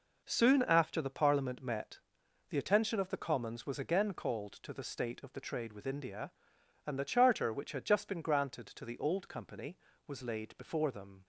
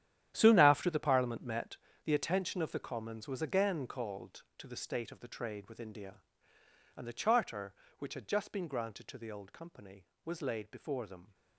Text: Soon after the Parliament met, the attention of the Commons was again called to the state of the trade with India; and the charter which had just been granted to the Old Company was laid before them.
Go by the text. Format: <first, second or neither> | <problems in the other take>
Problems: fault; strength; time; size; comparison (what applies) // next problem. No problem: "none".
first | gets quieter; strong; throughout; 15 dB